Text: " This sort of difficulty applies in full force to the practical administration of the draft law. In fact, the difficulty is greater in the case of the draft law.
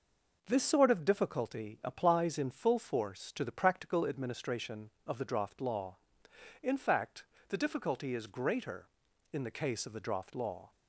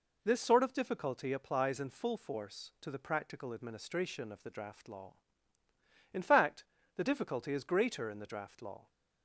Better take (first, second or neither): first